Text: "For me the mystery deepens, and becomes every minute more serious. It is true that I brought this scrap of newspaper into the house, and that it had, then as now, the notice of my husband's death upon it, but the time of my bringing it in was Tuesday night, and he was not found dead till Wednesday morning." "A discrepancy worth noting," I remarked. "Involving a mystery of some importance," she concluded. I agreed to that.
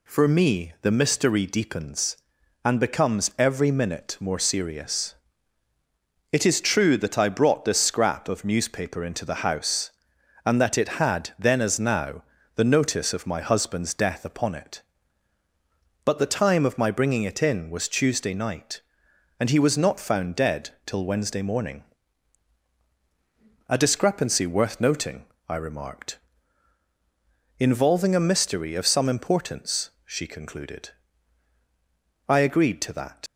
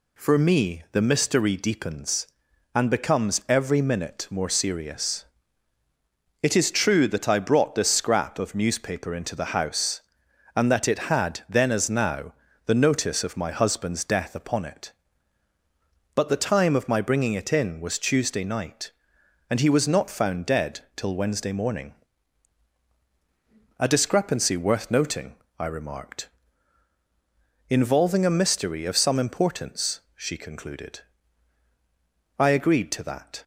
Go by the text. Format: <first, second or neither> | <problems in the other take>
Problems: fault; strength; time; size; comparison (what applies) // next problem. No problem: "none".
second | leaves "that" unfinished; at 33.2 s; 65 ms